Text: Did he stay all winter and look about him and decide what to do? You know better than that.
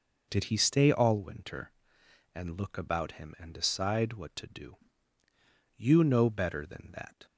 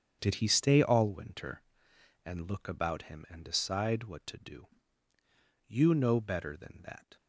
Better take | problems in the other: first | gets quieter; strong; throughout; 12 dB

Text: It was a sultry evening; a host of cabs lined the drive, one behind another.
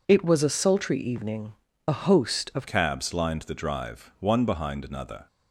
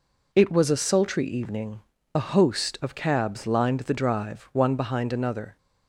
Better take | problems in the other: second | changes voice at "cabs"; from 2.6 s on; 2.6 s long

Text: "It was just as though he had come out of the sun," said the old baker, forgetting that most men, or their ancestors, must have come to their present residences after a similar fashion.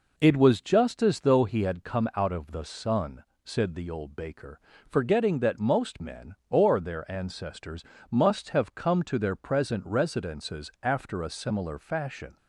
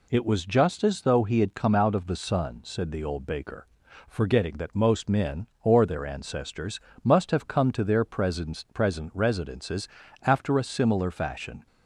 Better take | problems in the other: first | says "present" twice; at 8.7 s // pauses between "residences" and "after"; slight; at 9.8 s; 0.34 s long

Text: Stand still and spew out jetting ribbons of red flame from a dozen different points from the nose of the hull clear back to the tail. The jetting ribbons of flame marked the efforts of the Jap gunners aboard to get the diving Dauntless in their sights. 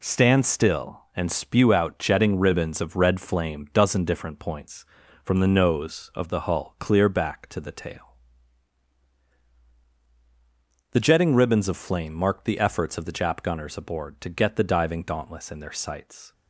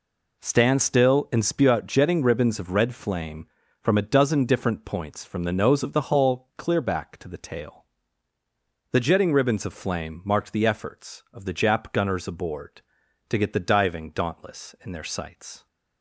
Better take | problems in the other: second | skips "from a"; at 3.6 s

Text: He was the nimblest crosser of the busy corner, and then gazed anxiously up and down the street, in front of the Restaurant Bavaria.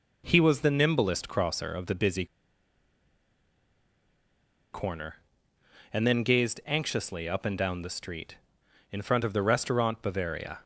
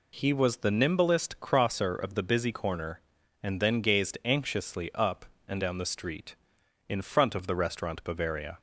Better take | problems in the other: second | pauses between "busy" and "corner"; strong; at 2.2 s; 2.4 s long

